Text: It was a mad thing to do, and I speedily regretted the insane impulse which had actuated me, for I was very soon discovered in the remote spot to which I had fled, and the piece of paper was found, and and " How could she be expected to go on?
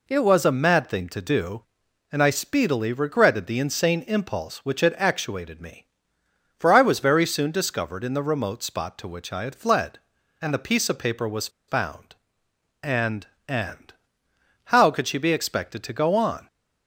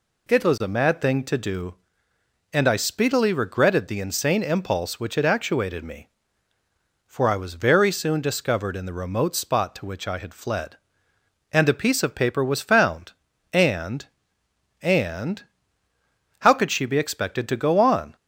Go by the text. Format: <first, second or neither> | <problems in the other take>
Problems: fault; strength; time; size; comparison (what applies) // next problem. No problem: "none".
second | pauses between "was" and "found"; slight; at 11.4 s; 0.19 s long